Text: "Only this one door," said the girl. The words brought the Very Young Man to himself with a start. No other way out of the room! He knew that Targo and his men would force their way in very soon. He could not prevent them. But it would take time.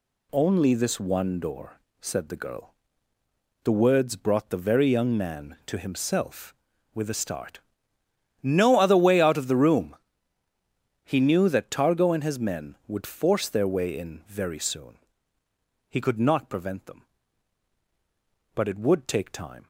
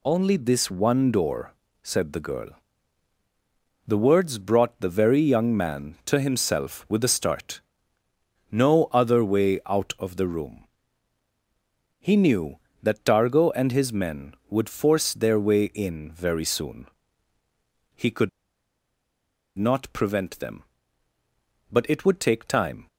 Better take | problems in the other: first | pauses between "could" and "not"; strong; at 18.2 s; 1.2 s long

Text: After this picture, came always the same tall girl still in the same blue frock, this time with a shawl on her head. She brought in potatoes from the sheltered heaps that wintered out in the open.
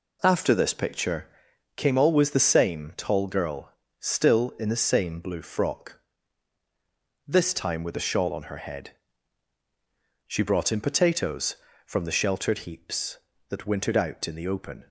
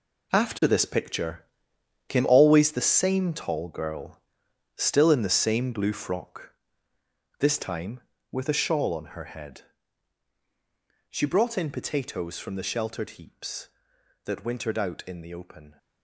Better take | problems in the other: first | gets quieter; strong; throughout; 11 dB // pauses between "girl" and "still"; noticeable; at 4.2 s; 0.56 s long; slight in the first

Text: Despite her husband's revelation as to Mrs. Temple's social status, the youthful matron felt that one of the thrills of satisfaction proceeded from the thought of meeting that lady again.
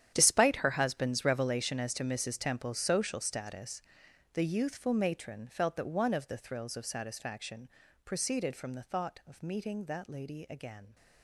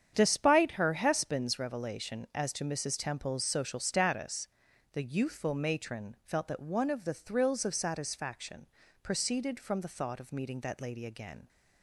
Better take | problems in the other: second | gets quieter; strong; throughout; 15.5 dB // starts louder than the rest; strong; until 1.1 s; 9.5 dB; strong in the second // pauses between "satisfaction" and "proceeded"; at 7.6 s; 0.38 s long; slight in the second

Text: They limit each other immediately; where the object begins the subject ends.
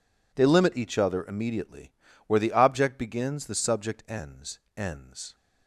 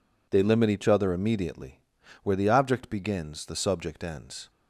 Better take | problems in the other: second | says "ends" twice; at 4.7 s

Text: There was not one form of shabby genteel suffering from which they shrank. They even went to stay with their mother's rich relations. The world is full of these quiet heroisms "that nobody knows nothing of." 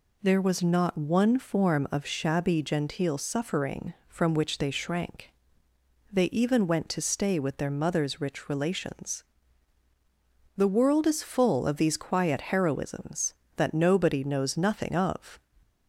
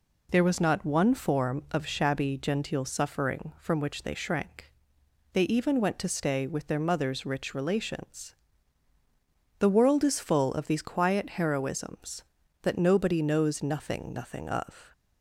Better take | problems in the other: first | says "nothing" twice; at 14.1 s

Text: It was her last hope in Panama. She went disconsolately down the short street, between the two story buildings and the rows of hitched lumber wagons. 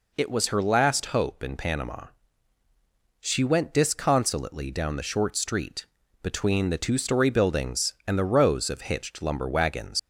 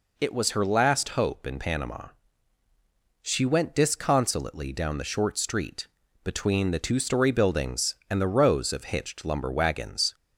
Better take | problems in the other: second | leaves "wagons" unfinished; at 9.9 s; 115 ms

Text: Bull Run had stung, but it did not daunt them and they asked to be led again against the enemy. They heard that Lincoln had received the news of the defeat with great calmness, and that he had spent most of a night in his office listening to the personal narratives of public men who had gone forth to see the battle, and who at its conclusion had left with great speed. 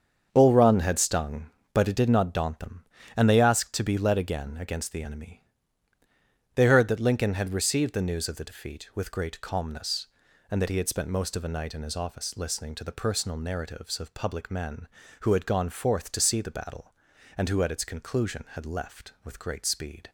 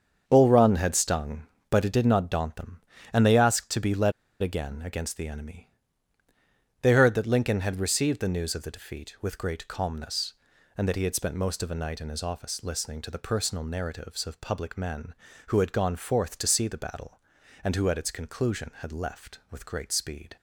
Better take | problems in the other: first | starts louder than the rest; until 1.2 s; 7 dB; also in the first // pauses between "led" and "again"; slight; at 4.1 s; 0.29 s long

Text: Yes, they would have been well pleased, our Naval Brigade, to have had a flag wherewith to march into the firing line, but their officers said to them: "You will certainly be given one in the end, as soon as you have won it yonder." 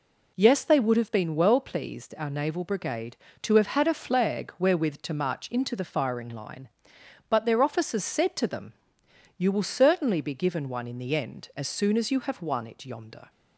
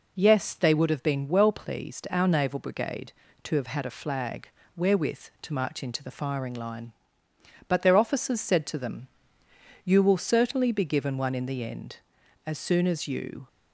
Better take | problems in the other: first | pauses between "flag" and "wherewith"; slight; at 4.4 s; 0.30 s long // stops before "have won it yonder"; at 13.4 s

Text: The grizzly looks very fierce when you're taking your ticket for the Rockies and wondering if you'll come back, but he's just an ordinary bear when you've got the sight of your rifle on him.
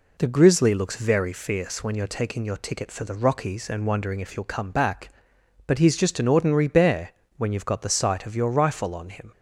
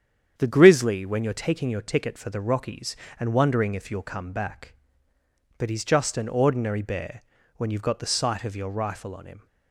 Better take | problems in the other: first | starts louder than the rest; strong; until 1.3 s; 8.5 dB // skips "looks very fierce"; at 1.0 s // pauses between "bear" and "when"; slight; at 7.2 s; 0.34 s long; slight in the first

